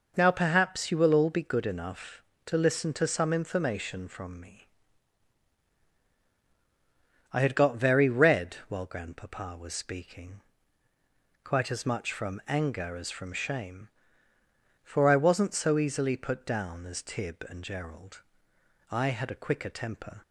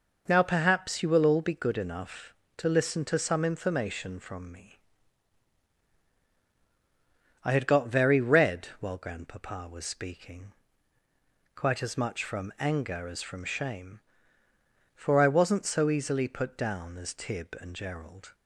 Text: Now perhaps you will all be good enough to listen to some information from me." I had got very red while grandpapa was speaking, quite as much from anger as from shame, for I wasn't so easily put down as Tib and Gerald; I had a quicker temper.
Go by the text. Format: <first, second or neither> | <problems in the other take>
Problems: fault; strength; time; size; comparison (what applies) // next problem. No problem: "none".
first | stops before "I had a quicker temper"; at 18.3 s